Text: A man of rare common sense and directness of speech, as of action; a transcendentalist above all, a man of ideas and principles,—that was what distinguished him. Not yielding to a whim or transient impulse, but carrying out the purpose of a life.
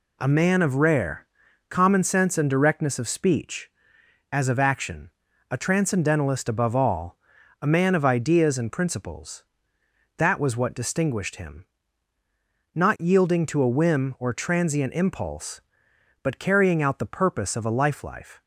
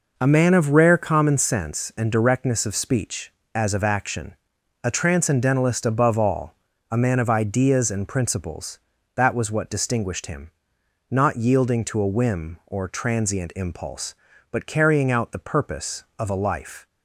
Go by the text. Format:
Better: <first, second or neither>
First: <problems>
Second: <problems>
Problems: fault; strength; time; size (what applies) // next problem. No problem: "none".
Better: second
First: pauses between "rare" and "common"; at 1.2 s; 0.44 s long // says "life" twice; at 18.0 s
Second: none